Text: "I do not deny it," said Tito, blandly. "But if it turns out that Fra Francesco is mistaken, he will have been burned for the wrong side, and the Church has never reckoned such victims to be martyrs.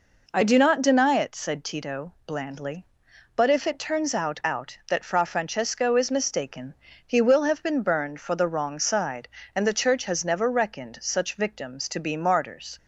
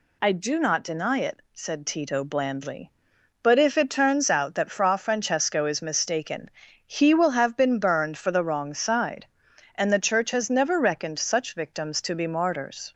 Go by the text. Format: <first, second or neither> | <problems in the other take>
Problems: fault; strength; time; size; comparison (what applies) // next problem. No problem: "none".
second | says "out" twice; at 4.4 s